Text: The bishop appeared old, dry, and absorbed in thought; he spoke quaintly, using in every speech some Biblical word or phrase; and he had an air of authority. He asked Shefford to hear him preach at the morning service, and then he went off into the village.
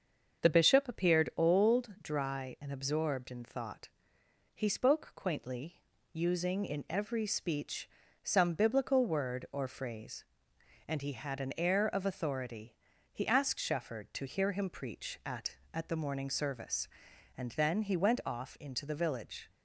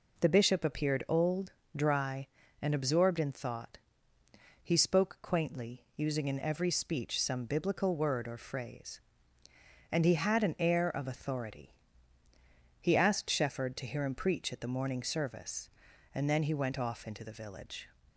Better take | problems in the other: second | starts louder than the rest; until 1.5 s; 7 dB // pauses between "speech" and "some"; slight; at 7.8 s; 0.34 s long // says "at" twice; at 15.7 s

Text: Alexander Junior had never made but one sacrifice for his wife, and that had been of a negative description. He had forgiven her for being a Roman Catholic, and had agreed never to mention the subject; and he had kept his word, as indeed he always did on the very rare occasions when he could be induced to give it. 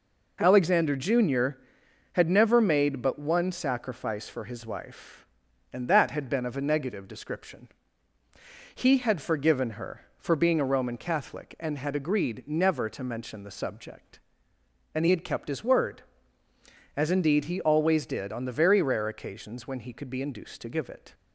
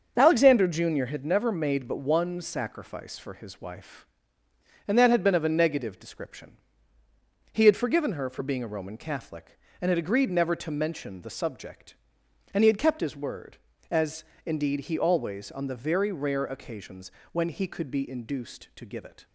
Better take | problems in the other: first | starts louder than the rest; until 1.1 s; 6.5 dB // pauses between "as" and "indeed"; slight; at 14.2 s; 0.22 s long // skips "did"; at 15.5 s // pauses between "occasions" and "when"; slight; at 17.1 s; 0.22 s long

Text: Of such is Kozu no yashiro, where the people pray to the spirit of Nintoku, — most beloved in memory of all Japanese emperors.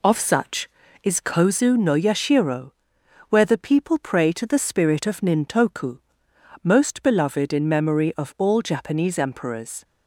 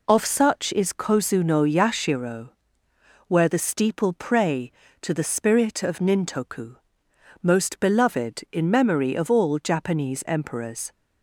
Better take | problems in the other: first | says "steeple" for "people"; at 3.5 s

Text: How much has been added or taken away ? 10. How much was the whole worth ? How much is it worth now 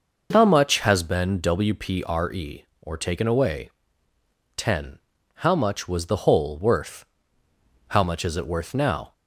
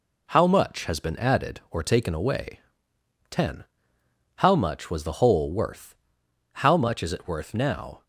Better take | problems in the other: second | says "wpre" for "added"; at 1.3 s

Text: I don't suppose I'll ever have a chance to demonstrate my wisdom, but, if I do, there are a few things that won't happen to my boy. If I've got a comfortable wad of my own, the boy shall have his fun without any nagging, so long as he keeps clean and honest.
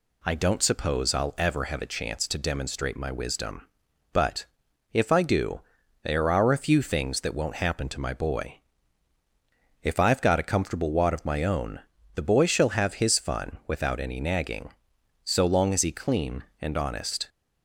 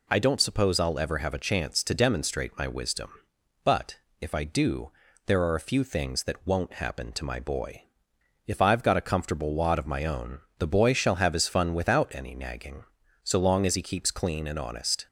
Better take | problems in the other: second | skips "keeps"; at 15.9 s

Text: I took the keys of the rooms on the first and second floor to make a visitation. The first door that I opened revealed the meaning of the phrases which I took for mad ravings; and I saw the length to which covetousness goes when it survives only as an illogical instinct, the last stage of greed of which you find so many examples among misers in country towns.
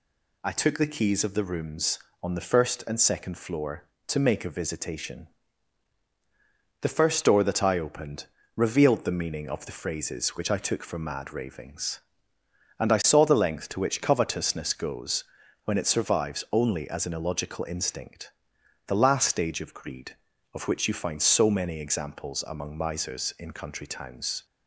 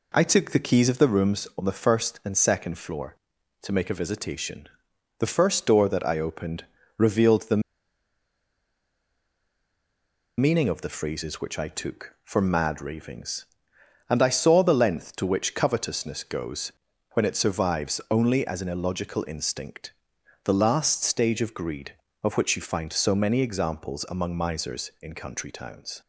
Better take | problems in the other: first | pauses between "opened" and "revealed"; slight; at 6.6 s; 0.34 s long; slight in the first // pauses between "the" and "meaning"; strong; at 7.6 s; 2.7 s long // pauses between "goes" and "when"; at 16.7 s; 0.40 s long; also in the first

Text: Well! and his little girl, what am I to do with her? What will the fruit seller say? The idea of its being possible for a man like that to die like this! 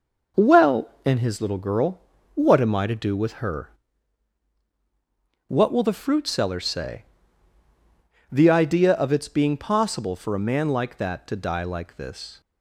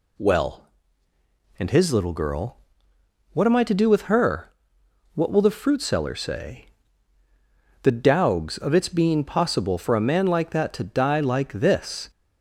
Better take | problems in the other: first | says "dowgs" for "idea"; at 7.9 s

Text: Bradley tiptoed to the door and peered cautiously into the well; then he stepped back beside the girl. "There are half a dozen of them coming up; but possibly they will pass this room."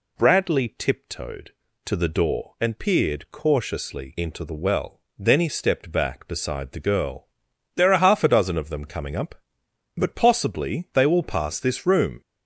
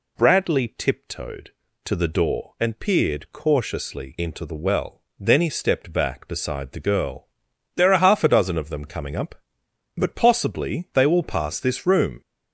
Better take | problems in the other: neither | none

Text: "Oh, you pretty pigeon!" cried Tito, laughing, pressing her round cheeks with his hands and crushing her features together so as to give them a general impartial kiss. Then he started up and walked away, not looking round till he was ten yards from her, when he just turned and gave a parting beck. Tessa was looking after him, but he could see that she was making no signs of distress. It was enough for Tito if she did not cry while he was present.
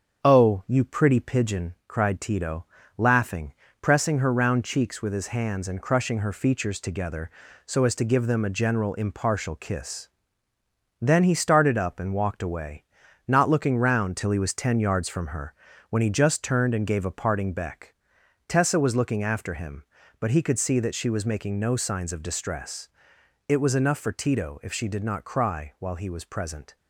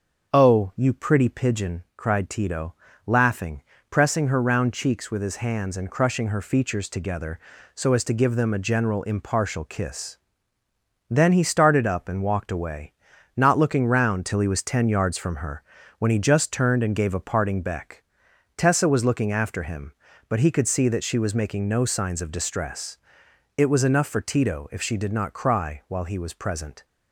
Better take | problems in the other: second | gets quieter; slight; throughout; 3 dB // starts louder than the rest; strong; until 1.3 s; 7.5 dB; also in the second

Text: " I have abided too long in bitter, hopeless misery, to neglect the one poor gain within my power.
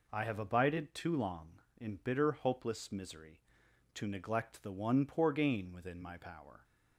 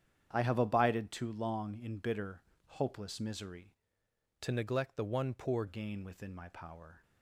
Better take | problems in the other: first | starts louder than the rest; strong; until 1.3 s; 9 dB // changes voice from "to" to "poor"; from 4.4 to 5.6 s; 1.2 s long

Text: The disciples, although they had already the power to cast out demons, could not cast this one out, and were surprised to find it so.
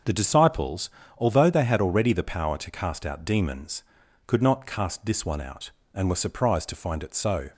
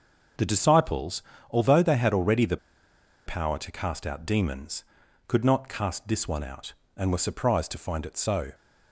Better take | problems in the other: first | pauses between "the" and "power"; noticeable; at 2.5 s; 0.70 s long

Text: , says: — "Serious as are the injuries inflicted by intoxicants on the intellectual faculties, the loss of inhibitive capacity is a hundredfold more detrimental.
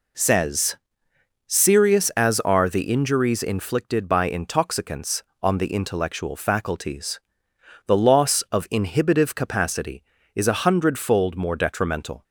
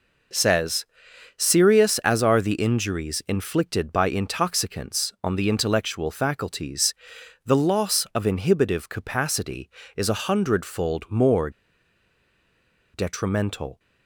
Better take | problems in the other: first | pauses between "more" and "detrimental"; strong; at 11.4 s; 1.4 s long

